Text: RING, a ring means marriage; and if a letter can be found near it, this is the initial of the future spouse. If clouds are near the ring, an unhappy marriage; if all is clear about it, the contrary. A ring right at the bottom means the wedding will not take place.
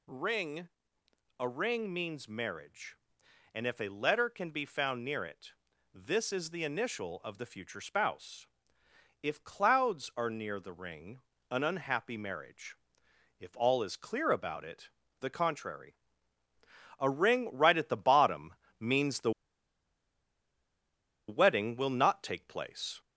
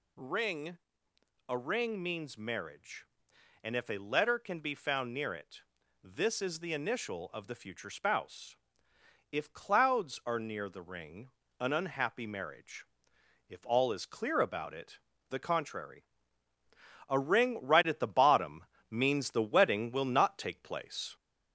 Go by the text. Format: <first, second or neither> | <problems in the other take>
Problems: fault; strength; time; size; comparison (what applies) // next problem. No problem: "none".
second | pauses between "bottom" and "means"; slight; at 18.5 s; 0.26 s long; slight in the second // pauses between "the" and "wedding"; strong; at 19.3 s; 1.9 s long